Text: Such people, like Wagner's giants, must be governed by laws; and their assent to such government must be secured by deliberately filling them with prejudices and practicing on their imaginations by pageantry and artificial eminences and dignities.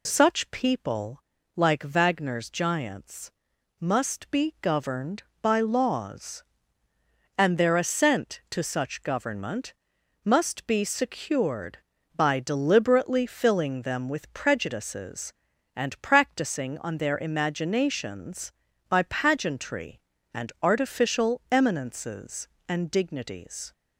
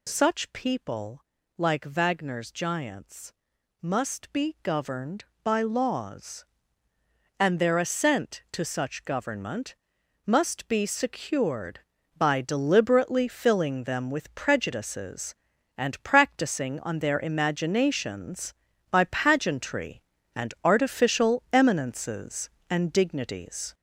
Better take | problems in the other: first | gets louder; noticeable; throughout; 5 dB // pauses between "government" and "must"; noticeable; at 9.7 s; 0.50 s long; noticeable in the first

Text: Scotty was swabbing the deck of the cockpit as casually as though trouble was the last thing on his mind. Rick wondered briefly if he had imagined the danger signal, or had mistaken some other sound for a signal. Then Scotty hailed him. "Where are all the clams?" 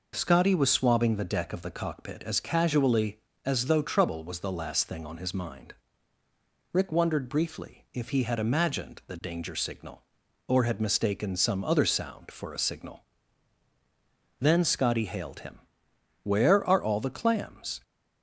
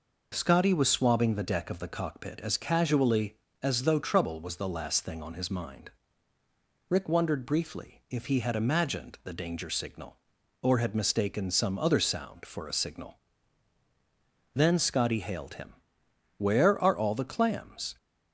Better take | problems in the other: neither | none

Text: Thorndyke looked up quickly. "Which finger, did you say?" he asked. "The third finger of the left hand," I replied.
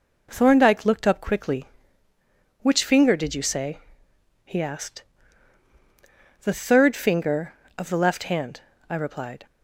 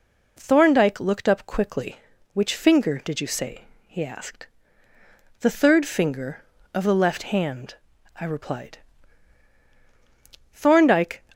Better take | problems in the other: first | goes on to say "Thorndyke"; noticeable; from 10.5 s on; 0.70 s long

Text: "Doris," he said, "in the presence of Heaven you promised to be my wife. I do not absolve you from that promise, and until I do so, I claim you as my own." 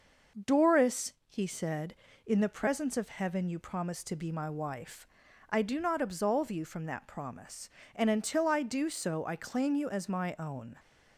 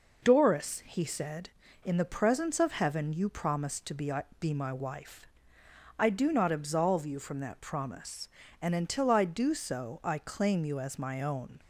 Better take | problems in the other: first | says "be" twice; at 4.3 s

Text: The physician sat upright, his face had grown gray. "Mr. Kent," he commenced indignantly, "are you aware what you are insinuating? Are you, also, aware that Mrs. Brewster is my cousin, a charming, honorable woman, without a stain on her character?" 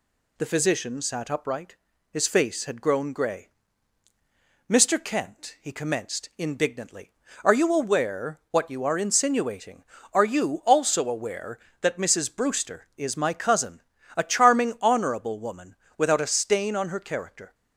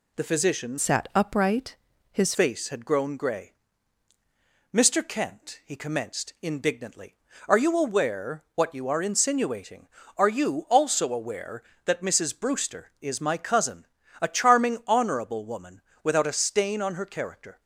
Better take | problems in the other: first | changes voice from "sat" to "his"; from 0.7 to 2.3 s; 1.6 s long

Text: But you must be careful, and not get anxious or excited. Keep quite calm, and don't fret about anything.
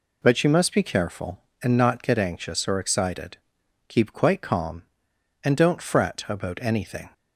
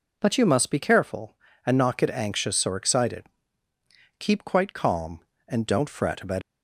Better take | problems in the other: first | stops before "anything"; at 6.4 s

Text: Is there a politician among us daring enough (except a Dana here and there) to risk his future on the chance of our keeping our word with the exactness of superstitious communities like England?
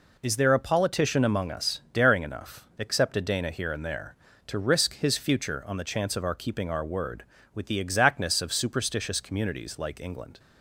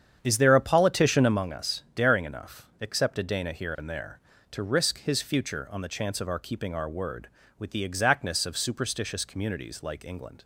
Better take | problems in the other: first | starts louder than the rest; strong; until 1.4 s; 8.5 dB

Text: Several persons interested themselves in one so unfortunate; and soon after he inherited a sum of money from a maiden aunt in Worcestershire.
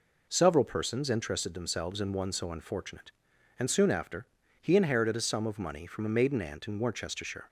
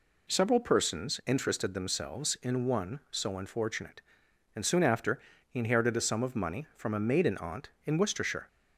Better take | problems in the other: neither | pauses between "after" and "he"; slight; the same in both

